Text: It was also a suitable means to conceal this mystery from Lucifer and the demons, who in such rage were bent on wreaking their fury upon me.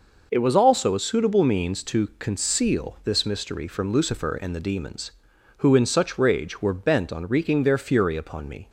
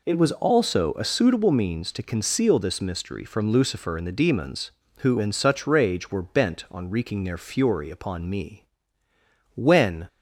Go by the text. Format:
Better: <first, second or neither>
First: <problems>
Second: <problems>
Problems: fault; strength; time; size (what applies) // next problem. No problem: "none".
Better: first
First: none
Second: goes on to say "When"; from 9.5 s on; 0.52 s long